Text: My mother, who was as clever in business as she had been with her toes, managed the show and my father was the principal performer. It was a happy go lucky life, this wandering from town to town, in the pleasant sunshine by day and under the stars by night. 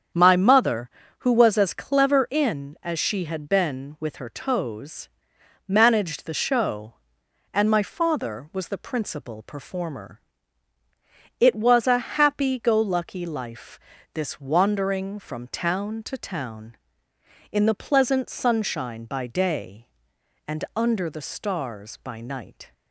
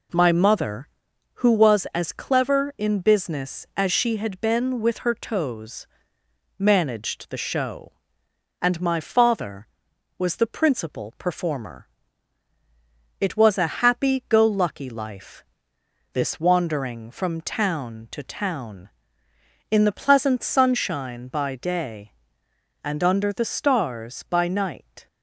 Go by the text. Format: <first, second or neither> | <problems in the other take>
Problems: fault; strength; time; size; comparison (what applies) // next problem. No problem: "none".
second | starts louder than the rest; strong; until 1.4 s; 7.5 dB // skips "business"; at 2.7 s